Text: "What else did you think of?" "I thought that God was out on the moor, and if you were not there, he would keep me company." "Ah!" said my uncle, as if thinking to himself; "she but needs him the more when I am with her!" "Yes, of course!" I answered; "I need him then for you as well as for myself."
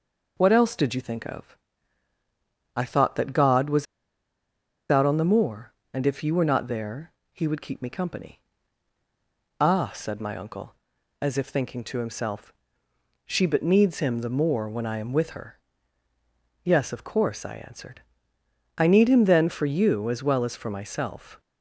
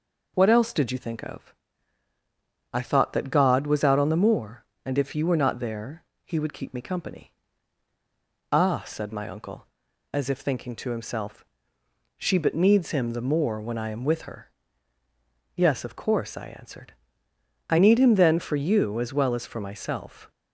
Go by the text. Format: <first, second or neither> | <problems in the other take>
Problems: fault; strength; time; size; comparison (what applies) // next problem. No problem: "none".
second | pauses between "was" and "out"; at 3.8 s; 1.0 s long